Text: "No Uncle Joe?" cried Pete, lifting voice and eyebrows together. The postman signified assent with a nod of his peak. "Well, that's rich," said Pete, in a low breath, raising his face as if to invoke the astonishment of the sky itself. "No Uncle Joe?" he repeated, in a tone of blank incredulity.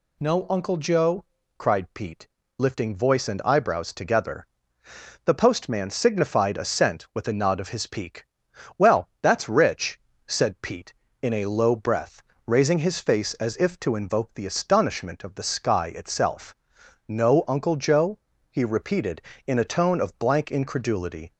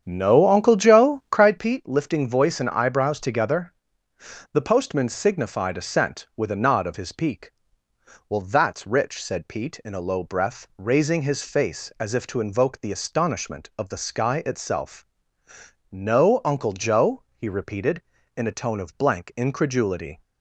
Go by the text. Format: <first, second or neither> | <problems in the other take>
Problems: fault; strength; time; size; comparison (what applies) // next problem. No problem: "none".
first | starts louder than the rest; strong; until 1.6 s; 8.5 dB